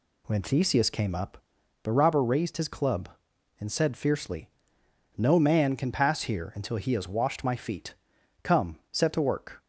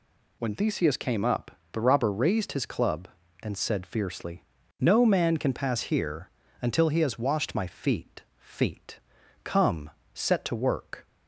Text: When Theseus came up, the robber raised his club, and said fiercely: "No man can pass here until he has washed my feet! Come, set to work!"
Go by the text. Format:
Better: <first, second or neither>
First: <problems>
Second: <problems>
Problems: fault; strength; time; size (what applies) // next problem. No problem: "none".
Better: first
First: none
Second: pauses between "here" and "until"; slight; at 6.2 s; 0.32 s long // says "feet" twice; at 8.3 s